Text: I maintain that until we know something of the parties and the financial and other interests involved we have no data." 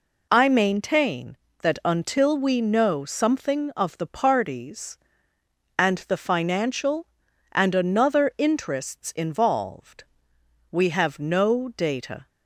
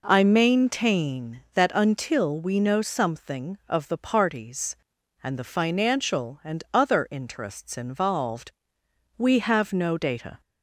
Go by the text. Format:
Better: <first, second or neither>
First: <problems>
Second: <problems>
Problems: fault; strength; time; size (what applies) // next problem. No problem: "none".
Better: second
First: says "another" for "other"; at 7.7 s // pauses between "involved" and "we"; noticeable; at 10.0 s; 0.66 s long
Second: pauses between "involved" and "we"; noticeable; at 8.5 s; 0.64 s long